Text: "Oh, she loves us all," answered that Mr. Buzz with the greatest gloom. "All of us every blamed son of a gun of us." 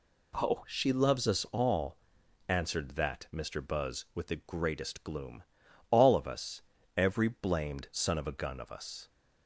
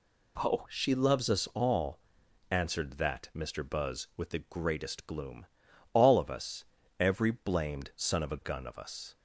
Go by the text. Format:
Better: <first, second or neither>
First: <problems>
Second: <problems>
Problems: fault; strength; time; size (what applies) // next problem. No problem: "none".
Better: neither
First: pauses between "us" and "every"; slight; at 6.6 s; 0.36 s long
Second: pauses between "us" and "every"; slight; at 6.6 s; 0.36 s long